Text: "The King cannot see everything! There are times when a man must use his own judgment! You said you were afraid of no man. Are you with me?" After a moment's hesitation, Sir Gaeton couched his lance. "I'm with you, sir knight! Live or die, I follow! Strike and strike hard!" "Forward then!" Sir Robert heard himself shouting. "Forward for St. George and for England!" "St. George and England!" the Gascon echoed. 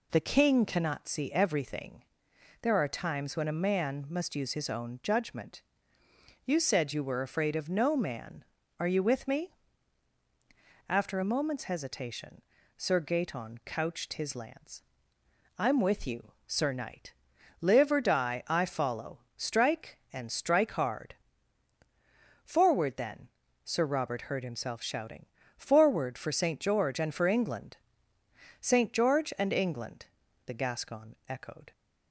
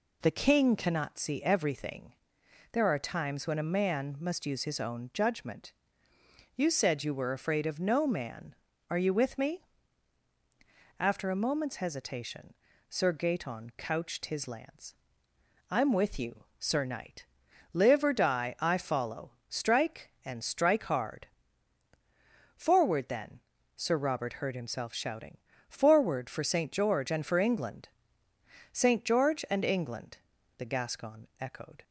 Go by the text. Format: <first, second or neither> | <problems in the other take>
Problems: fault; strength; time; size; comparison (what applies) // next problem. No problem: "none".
neither | none